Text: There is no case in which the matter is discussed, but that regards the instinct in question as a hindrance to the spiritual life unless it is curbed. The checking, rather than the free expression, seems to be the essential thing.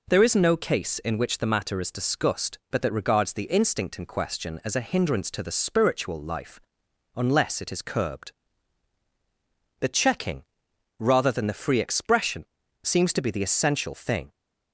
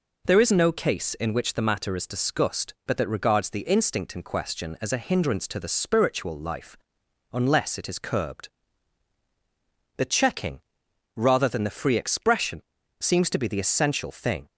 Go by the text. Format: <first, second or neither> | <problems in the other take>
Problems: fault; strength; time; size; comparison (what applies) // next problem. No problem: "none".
neither | pauses between "life" and "unless"; noticeable; the same in both